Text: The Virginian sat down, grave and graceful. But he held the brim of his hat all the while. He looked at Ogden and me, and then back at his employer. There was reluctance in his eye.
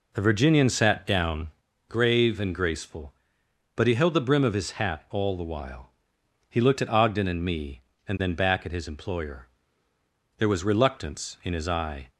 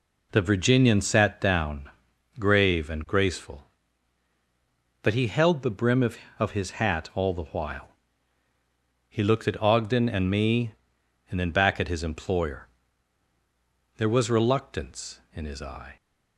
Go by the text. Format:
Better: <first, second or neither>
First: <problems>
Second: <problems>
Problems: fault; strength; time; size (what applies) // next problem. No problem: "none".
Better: first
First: none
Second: says "of" twice; at 6.3 s